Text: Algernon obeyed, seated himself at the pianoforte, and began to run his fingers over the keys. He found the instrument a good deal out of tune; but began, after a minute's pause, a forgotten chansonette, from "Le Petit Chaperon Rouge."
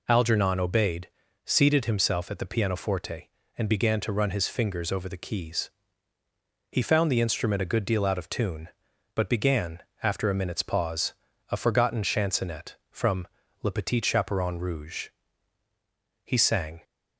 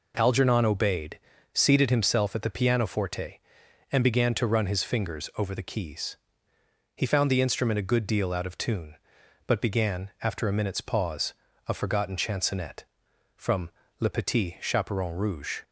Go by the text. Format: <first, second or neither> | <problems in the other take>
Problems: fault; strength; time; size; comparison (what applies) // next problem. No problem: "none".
second | pauses between "from" and "Le"; slight; at 13.2 s; 0.34 s long; slight in the second // goes on to say "He sang"; from 16.2 s on; 0.58 s long